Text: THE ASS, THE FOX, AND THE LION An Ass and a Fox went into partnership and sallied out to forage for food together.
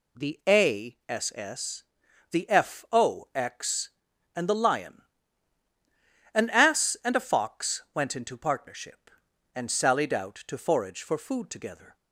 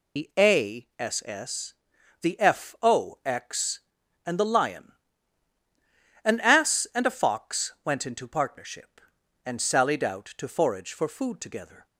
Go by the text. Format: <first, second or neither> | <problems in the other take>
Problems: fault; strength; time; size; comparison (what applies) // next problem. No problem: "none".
first | loses the start of "THE"; at 0.1 s; 90 ms // pauses between "LION" and "An"; strong; at 4.9 s; 1.3 s long; strong in the first